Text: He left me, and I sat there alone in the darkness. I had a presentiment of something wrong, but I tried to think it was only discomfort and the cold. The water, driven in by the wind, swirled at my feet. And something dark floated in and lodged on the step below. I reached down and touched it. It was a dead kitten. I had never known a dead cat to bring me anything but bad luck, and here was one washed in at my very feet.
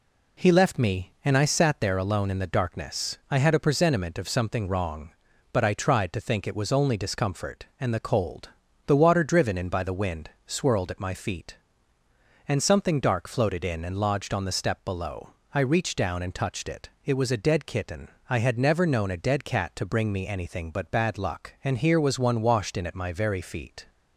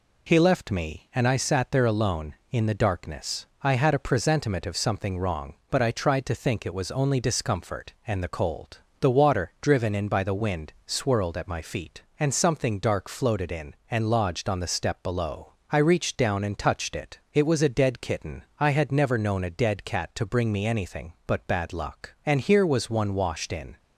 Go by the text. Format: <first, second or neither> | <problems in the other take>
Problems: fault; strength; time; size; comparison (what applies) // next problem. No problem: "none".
first | stops before "at my very feet"; at 23.7 s